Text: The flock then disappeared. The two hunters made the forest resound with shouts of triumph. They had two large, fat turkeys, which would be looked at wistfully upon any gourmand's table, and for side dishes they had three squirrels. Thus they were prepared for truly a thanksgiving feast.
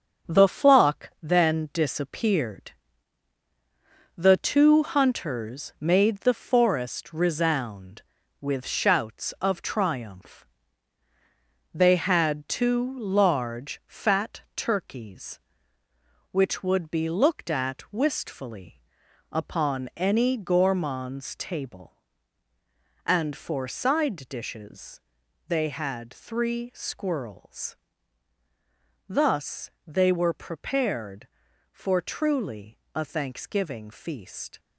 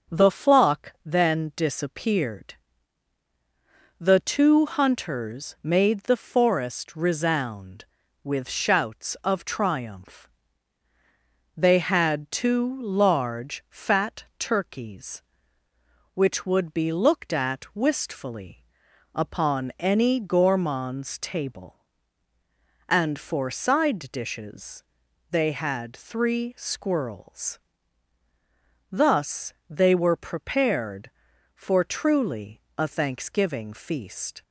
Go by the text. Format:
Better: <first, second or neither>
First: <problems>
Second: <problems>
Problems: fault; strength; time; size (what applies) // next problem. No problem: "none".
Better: second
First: gets quieter; throughout; 6.5 dB // starts louder than the rest; until 1.3 s; 7 dB // pauses between "wistfully" and "upon"; noticeable; at 18.8 s; 0.50 s long // pauses between "dishes" and "they"; noticeable; at 25.0 s; 0.48 s long // pauses between "Thus" and "they"; slight; at 29.6 s; 0.16 s long // pauses between "truly" and "a"; slight; at 32.7 s; 0.16 s long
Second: starts louder than the rest; until 1.2 s; 6.5 dB // pauses between "wistfully" and "upon"; noticeable; at 18.6 s; 0.50 s long // pauses between "dishes" and "they"; noticeable; at 24.8 s; 0.48 s long // pauses between "Thus" and "they"; slight; at 29.5 s; 0.16 s long // pauses between "truly" and "a"; slight; at 32.6 s; 0.16 s long